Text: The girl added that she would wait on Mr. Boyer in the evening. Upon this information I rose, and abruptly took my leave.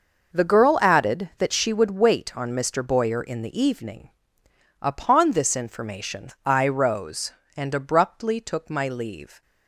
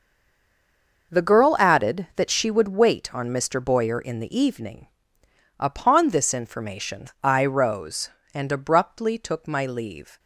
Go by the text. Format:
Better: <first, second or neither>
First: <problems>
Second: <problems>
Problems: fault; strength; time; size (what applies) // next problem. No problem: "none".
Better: first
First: pauses between "information" and "I"; slight; at 6.2 s; 0.16 s long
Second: stays silent before the first word; until 1.1 s; 1.1 s long // pauses between "information" and "I"; slight; at 7.0 s; 0.16 s long